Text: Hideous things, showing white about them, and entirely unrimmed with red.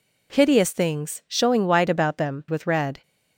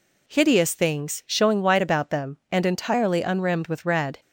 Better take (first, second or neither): second